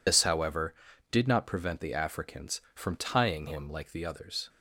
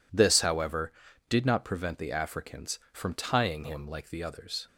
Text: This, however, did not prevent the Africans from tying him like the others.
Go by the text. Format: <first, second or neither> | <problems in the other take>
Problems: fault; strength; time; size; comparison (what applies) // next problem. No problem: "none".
second | loses the start of "This"; at 0.0 s; 135 ms